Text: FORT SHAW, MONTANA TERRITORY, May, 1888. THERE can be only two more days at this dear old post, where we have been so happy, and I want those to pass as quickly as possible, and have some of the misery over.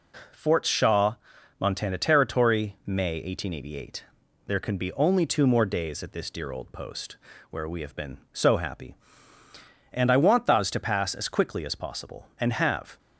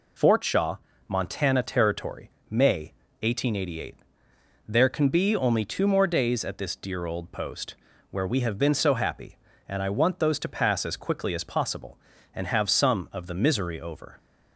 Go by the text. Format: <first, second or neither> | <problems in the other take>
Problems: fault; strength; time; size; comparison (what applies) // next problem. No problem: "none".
second | stops before "some of the misery over"; at 12.9 s